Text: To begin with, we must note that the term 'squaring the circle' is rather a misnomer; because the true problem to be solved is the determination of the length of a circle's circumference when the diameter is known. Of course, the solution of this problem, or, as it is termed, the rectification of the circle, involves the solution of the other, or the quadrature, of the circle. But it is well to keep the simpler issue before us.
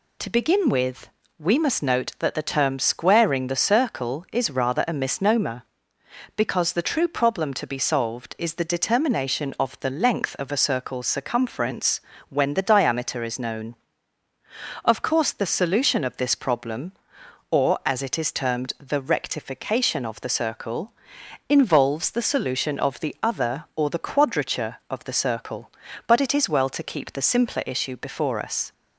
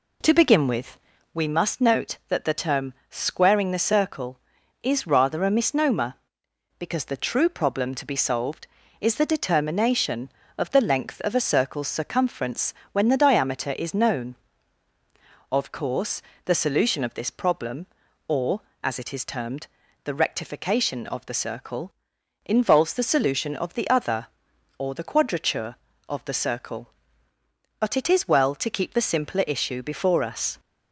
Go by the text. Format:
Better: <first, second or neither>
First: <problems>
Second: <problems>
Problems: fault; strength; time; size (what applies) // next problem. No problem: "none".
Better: first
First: pauses between "circumference" and "when"; slight; at 12.0 s; 0.30 s long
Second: starts louder than the rest; slight; until 1.5 s; 2.5 dB // pauses between "term" and "squaring"; slight; at 2.9 s; 0.16 s long // pauses between "circumference" and "when"; slight; at 12.7 s; 0.20 s long